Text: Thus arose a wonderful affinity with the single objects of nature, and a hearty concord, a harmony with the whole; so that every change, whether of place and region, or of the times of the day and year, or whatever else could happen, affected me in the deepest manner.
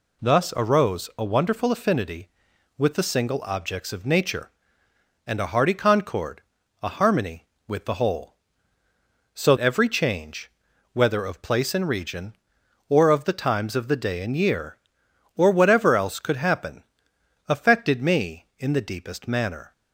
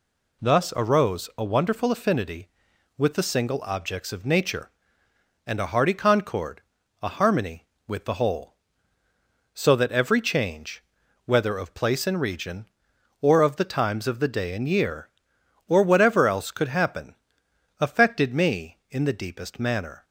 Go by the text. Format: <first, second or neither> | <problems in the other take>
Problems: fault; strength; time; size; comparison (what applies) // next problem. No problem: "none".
second | skips "that"; at 9.5 s